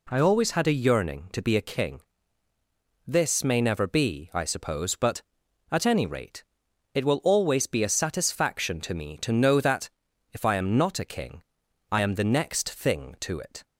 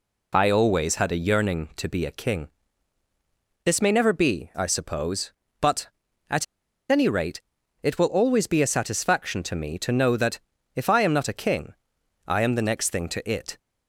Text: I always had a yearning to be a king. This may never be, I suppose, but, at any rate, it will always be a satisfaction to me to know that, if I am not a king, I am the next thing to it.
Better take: first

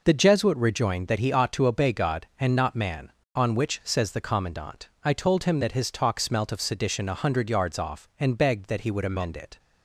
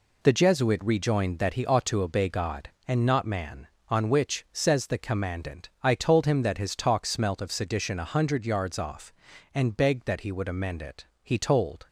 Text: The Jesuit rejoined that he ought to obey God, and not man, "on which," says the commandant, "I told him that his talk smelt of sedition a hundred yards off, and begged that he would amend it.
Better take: first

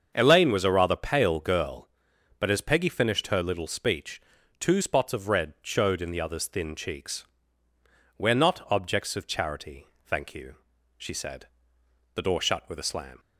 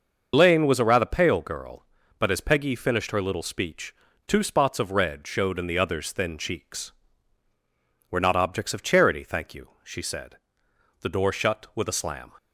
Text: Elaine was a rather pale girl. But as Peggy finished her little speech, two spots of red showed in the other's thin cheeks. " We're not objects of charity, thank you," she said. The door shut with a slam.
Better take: first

